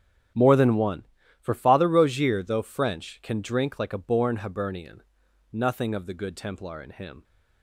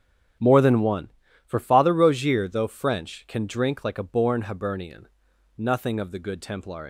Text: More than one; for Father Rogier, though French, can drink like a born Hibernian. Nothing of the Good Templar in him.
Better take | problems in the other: first | starts louder than the rest; strong; until 1.7 s; 8.5 dB; strong in the first // stops before "in him"; at 6.8 s

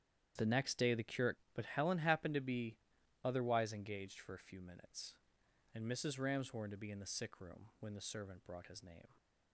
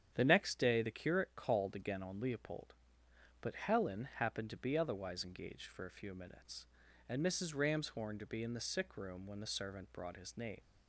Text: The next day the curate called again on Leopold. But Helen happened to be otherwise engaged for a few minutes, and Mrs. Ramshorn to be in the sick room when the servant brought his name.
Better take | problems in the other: second | starts louder than the rest; strong; until 1.3 s; 9.5 dB; strong in the second // skips "called again on Leopold"; at 1.4 s // pauses between "be" and "otherwise"; noticeable; at 2.7 s; 0.46 s long

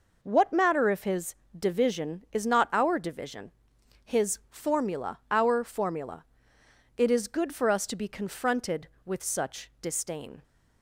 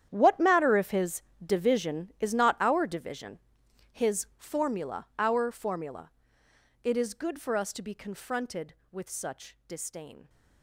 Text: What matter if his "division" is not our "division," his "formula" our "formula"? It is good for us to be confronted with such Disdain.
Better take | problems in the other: first | gets quieter; strong; throughout; 16 dB // pauses between "his" and "division"; slight; at 1.2 s; 0.24 s long; slight in the first

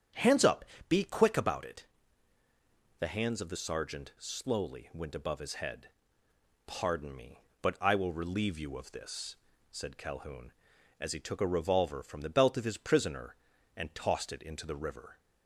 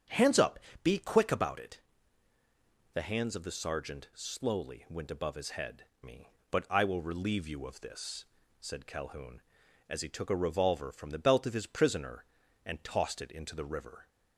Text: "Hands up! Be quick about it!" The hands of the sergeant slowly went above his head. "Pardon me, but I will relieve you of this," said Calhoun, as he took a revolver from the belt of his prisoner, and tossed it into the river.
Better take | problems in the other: first | starts louder than the rest; strong; until 1.3 s; 8 dB; strong in the first // skips "Pardon"; at 5.9 s

